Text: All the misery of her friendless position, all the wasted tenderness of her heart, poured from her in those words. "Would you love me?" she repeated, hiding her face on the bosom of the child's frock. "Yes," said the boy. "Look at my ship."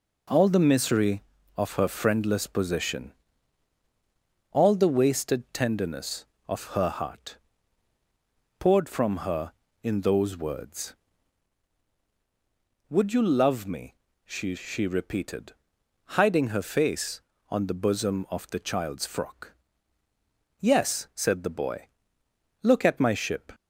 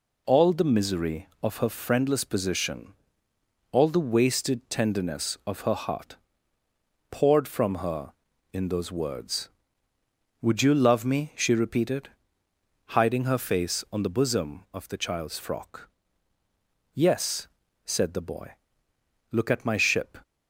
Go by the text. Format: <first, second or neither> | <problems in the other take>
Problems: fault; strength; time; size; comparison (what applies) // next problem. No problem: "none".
second | says "she" twice; at 14.5 s